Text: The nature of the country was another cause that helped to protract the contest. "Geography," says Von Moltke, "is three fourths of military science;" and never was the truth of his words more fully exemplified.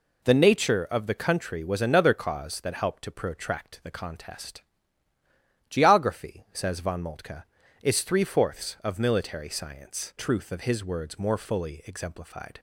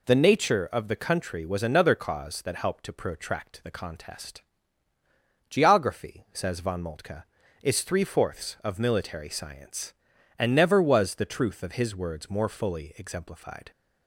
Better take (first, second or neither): second